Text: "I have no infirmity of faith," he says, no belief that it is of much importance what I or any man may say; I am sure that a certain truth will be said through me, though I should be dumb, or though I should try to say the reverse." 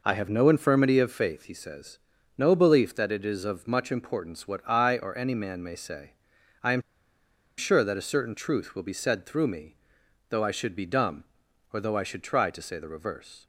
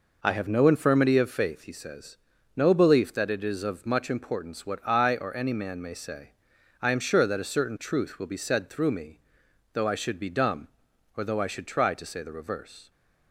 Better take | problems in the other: second | pauses between "am" and "sure"; noticeable; at 6.8 s; 0.77 s long

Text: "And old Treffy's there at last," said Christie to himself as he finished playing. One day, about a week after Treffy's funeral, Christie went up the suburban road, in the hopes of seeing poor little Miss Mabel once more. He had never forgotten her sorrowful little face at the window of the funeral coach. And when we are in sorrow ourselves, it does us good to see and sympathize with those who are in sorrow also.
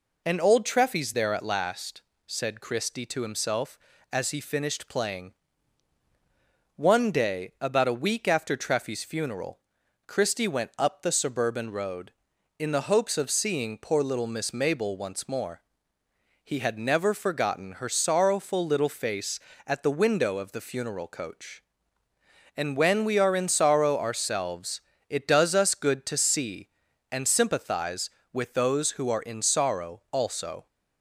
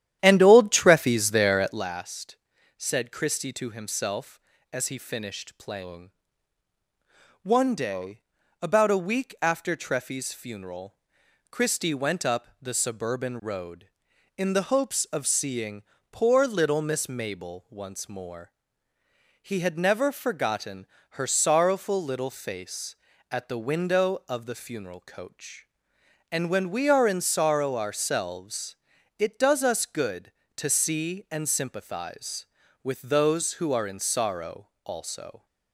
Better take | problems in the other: first | starts louder than the rest; strong; until 1.9 s; 11 dB // pauses between "seeing" and "poor"; slight; at 15.8 s; 0.28 s long // pauses between "forgotten" and "her"; slight; at 20.8 s; 0.26 s long

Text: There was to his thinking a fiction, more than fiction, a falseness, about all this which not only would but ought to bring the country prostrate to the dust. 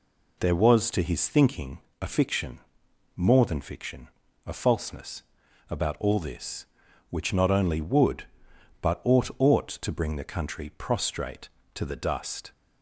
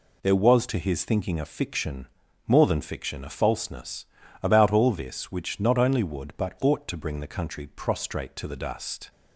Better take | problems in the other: second | pauses between "thinking" and "a"; slight; at 1.7 s; 0.20 s long // says "ought" twice; at 9.3 s

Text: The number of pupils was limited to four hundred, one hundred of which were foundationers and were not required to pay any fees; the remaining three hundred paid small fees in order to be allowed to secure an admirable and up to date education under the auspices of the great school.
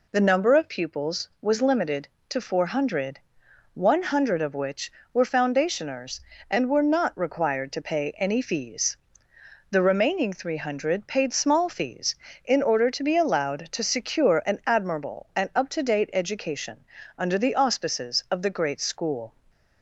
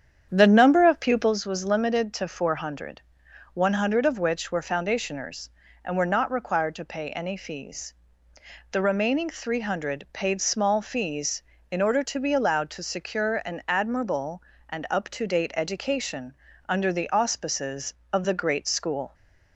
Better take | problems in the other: first | starts louder than the rest; strong; until 1.4 s; 8.5 dB // pauses between "education" and "under"; slight; at 16.3 s; 0.32 s long; slight in the first

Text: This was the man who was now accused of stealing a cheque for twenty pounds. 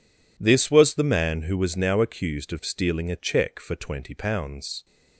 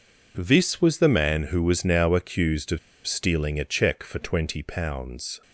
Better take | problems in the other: first | pauses between "of" and "stealing"; slight; at 2.7 s; 0.28 s long

